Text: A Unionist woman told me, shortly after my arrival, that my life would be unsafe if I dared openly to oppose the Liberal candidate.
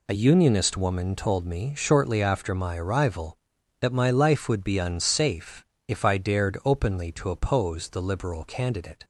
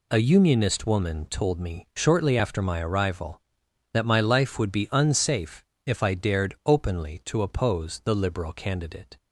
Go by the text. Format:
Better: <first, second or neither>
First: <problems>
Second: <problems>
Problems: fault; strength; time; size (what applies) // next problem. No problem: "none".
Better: neither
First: pauses between "unsafe" and "if"; slight; at 5.6 s; 0.22 s long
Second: pauses between "unsafe" and "if"; slight; at 5.6 s; 0.22 s long